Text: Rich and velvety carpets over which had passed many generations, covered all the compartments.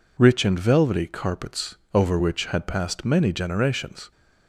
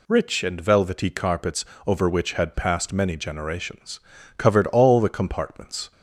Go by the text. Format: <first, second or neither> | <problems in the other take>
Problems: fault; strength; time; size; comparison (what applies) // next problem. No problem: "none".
second | pauses between "carpets" and "over"; slight; at 1.7 s; 0.18 s long; slight in the second // stops before "covered all the compartments"; at 4.1 s